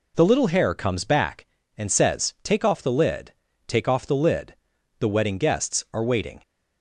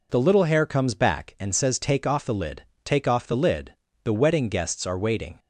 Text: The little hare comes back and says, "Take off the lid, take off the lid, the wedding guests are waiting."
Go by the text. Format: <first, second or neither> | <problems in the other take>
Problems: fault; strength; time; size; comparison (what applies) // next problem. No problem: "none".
neither | none